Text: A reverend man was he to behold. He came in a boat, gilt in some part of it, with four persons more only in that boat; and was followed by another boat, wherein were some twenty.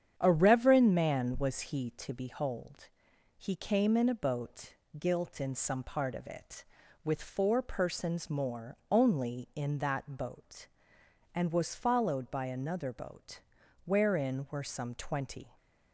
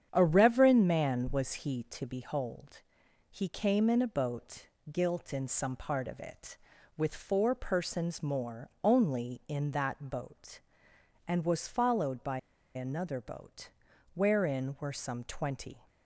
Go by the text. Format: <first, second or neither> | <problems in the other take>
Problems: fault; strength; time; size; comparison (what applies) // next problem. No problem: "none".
first | starts louder than the rest; strong; until 1.1 s; 8.5 dB; strong in the first // pauses between "by" and "another"; slight; at 12.3 s; 0.35 s long